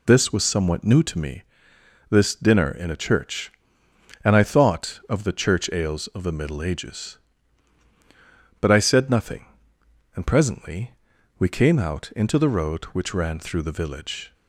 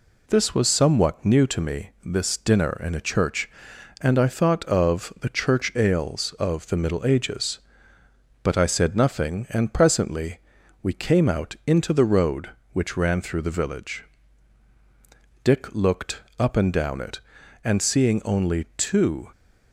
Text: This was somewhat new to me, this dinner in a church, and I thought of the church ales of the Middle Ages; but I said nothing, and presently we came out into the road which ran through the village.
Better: first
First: pauses between "presently" and "we"; at 10.9 s; 0.44 s long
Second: pauses between "presently" and "we"; at 10.3 s; 0.44 s long // goes on to say "Dick looked up and down it and seeing only two"; strong; from 15.4 s on; 3.8 s long

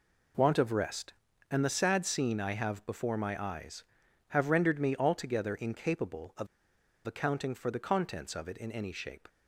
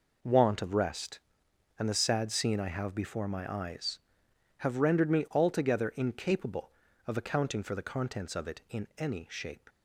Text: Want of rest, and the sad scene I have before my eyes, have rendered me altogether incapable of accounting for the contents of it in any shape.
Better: second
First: pauses between "of" and "accounting"; noticeable; at 6.4 s; 0.60 s long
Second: none

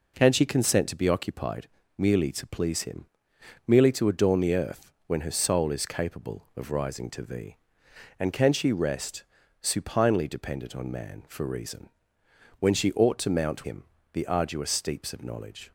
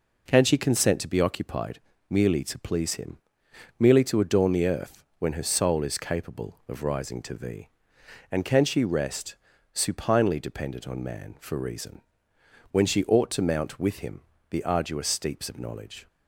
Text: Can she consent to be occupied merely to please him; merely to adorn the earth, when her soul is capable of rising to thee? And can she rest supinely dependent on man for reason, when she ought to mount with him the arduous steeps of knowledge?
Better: second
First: pauses between "occupied" and "merely"; slight; at 1.6 s; 0.30 s long // pauses between "rest" and "supinely"; slight; at 9.2 s; 0.36 s long // skips "with"; at 13.6 s // pauses between "him" and "the"; slight; at 13.8 s; 0.30 s long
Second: pauses between "occupied" and "merely"; slight; at 1.7 s; 0.30 s long // pauses between "rest" and "supinely"; slight; at 9.3 s; 0.36 s long // pauses between "him" and "the"; slight; at 14.2 s; 0.30 s long

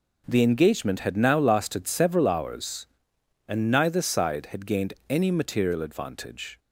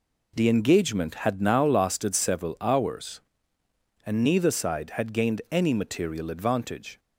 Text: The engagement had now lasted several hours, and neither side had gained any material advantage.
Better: neither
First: none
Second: none

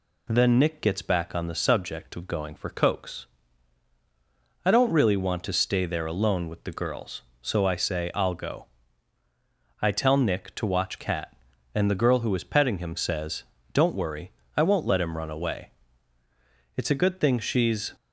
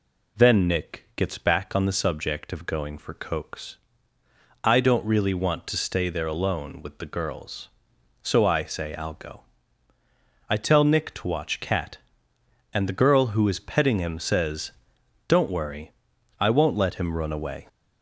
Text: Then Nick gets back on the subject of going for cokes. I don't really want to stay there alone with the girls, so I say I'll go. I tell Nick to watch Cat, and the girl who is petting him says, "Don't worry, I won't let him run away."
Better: second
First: goes on to say "It's a good thing she's"; noticeable; from 16.7 s on; 1.1 s long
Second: none

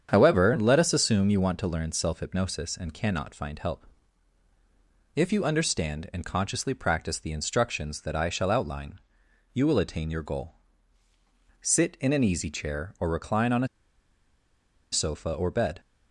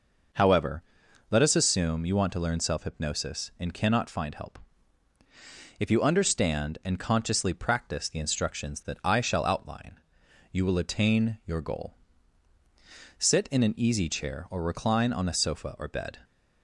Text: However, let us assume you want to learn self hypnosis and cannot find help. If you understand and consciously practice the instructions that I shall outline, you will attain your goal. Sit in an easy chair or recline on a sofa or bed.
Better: second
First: starts louder than the rest; strong; until 1.1 s; 8 dB // pauses between "a" and "sofa"; at 13.6 s; 1.2 s long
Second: none

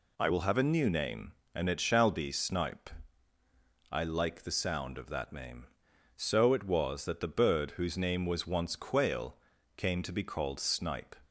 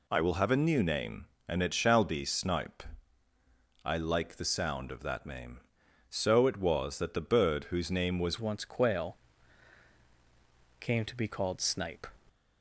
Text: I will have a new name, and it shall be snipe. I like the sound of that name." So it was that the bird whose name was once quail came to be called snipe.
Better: first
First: pauses between "quail" and "came"; at 9.3 s; 0.40 s long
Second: changes voice at "once"; from 8.4 s on; 3.6 s long // pauses between "quail" and "came"; strong; at 9.1 s; 1.6 s long

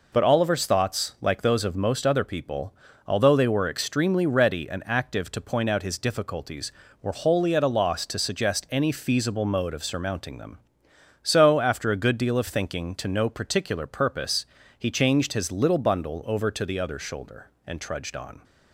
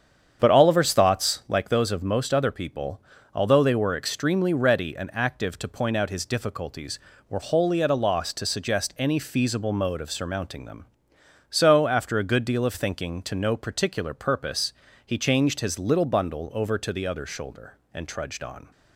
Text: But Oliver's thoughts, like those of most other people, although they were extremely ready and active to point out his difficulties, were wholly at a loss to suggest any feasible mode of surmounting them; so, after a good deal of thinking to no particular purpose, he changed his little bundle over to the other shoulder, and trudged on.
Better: first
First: none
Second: starts louder than the rest; strong; until 1.5 s; 8 dB

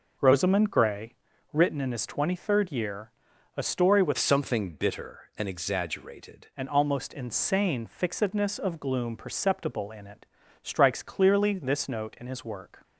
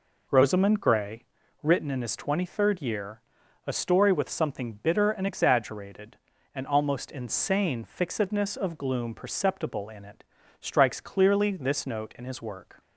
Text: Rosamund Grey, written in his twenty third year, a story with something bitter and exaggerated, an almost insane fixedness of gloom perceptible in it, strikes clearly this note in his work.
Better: second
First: changes voice from "something" to "exaggerated"; from 4.1 to 6.4 s; 2.3 s long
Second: none

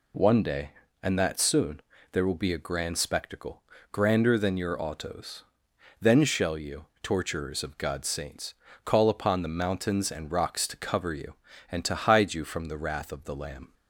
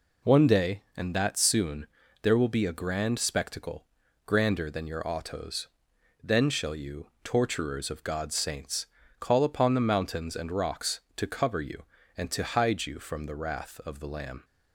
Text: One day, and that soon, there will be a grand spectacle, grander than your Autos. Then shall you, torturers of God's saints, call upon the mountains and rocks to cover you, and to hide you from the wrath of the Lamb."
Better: neither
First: none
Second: none

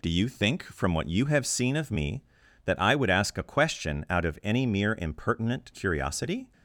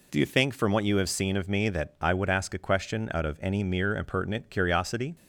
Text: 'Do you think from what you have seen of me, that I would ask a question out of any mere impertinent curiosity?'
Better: neither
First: none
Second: none

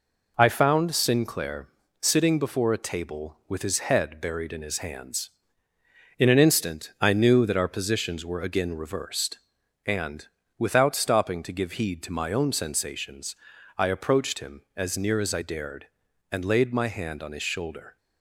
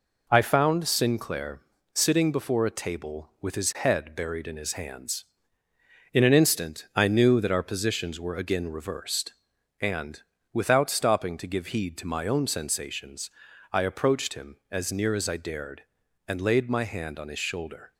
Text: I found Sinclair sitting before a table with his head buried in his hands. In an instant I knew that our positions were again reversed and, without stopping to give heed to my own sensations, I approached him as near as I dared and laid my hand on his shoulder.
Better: neither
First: pauses between "Sinclair" and "sitting"; slight; at 1.6 s; 0.32 s long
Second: pauses between "Sinclair" and "sitting"; slight; at 1.6 s; 0.32 s long

